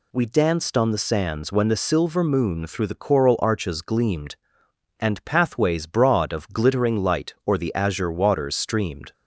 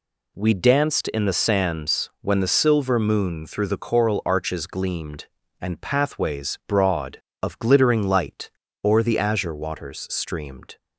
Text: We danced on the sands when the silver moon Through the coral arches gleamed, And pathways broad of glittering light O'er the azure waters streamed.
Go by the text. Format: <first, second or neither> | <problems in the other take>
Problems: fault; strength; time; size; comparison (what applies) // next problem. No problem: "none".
first | says "in" for "on"; at 1.0 s // pauses between "light" and "O'er"; slight; at 8.4 s; 0.34 s long